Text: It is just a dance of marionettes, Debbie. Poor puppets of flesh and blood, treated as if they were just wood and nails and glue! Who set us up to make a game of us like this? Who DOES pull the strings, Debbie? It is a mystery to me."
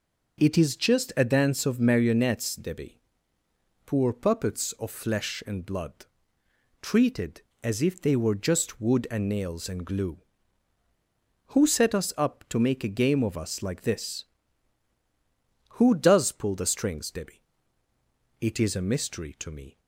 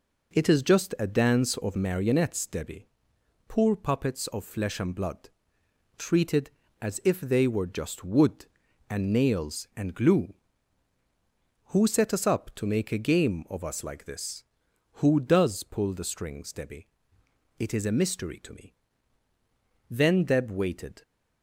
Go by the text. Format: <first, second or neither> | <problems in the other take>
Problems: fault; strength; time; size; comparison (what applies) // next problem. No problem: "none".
first | goes on to say "Then Deb waited"; noticeable; from 19.8 s on; 1.1 s long